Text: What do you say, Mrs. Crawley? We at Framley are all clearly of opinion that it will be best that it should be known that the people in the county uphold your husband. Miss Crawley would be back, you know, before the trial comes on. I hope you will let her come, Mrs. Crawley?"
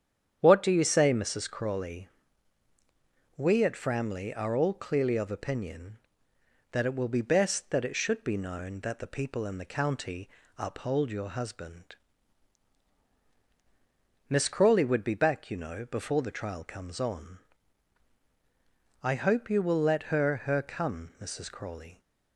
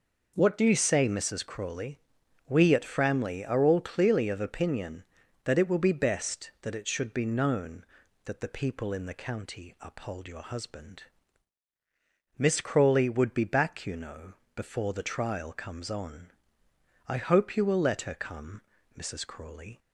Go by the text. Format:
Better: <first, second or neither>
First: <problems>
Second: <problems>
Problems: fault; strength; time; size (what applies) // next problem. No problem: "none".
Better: second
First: starts louder than the rest; strong; until 1.4 s; 9 dB // pauses between "county" and "uphold"; slight; at 10.2 s; 0.30 s long // says "her" twice; at 20.4 s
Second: none